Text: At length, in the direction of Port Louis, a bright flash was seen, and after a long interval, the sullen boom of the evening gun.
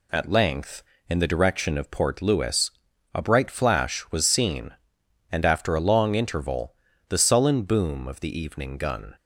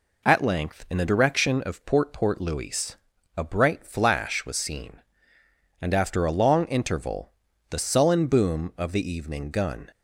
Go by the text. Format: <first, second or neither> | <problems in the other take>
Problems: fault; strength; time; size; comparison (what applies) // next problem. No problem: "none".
first | says "Port" twice; at 2.1 s